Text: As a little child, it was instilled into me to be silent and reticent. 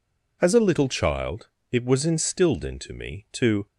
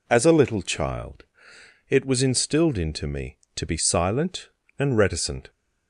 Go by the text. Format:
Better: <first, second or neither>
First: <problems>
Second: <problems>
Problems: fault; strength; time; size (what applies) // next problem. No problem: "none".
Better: second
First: stops before "be silent and reticent"; at 3.6 s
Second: none